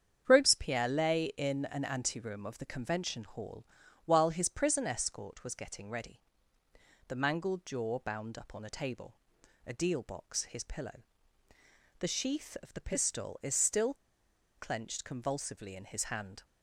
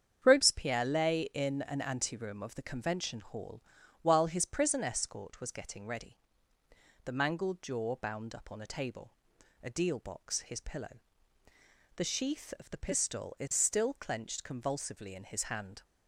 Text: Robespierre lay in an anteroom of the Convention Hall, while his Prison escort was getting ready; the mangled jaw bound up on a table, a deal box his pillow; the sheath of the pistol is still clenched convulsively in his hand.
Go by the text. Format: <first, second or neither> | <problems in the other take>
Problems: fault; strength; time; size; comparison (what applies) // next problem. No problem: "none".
second | starts louder than the rest; strong; until 1.2 s; 8 dB; strong in the second // pauses between "still" and "clenched"; noticeable; at 13.9 s; 0.63 s long